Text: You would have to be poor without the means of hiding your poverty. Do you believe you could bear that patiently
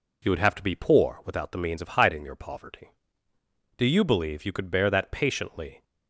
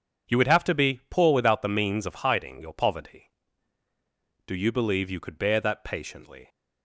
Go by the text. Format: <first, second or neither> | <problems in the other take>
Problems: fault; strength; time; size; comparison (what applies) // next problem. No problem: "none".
neither | none